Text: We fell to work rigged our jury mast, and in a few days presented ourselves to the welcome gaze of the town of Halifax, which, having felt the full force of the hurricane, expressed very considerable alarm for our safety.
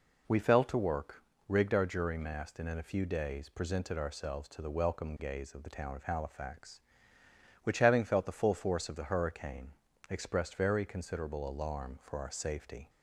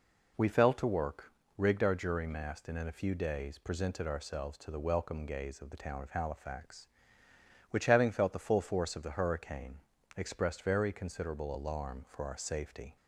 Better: neither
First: pauses between "work" and "rigged"; slight; at 1.2 s; 0.26 s long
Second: pauses between "work" and "rigged"; slight; at 1.3 s; 0.26 s long

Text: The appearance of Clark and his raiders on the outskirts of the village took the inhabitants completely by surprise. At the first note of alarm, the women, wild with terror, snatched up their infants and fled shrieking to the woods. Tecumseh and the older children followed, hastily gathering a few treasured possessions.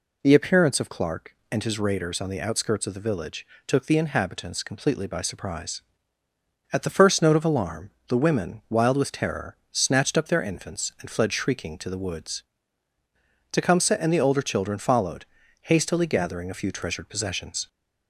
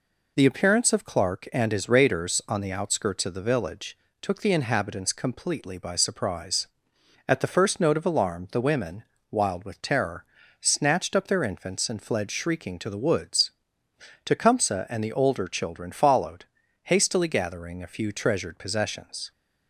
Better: neither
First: pauses between "village" and "took"; slight; at 3.4 s; 0.20 s long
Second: pauses between "village" and "took"; slight; at 3.9 s; 0.24 s long

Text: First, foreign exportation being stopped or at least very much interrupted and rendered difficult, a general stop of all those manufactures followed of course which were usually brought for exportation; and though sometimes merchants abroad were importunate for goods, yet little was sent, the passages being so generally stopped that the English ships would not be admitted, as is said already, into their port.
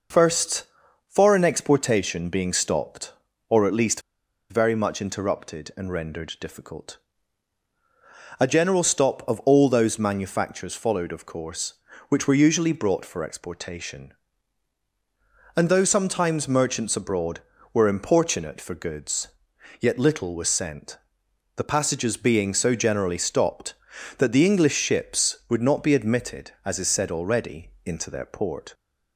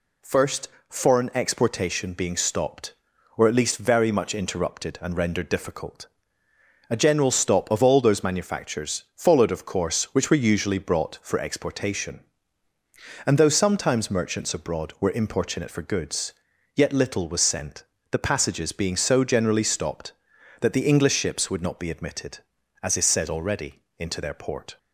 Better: second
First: pauses between "least" and "very"; noticeable; at 4.0 s; 0.48 s long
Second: none

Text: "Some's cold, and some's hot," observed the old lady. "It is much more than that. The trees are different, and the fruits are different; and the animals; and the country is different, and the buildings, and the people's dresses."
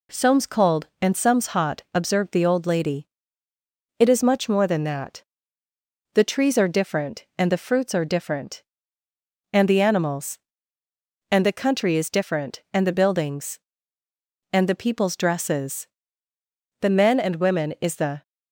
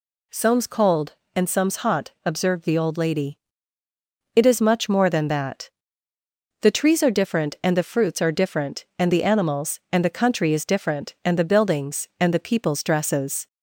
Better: second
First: goes on to say "The men and women is the"; from 16.8 s on; 1.4 s long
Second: none

